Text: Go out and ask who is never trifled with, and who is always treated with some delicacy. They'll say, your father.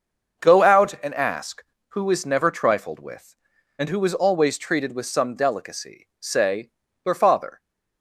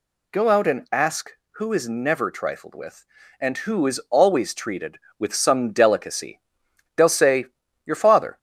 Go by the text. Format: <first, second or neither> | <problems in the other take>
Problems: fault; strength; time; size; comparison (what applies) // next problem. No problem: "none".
second | starts louder than the rest; noticeable; until 1.5 s; 6 dB // skips "They'll"; at 6.1 s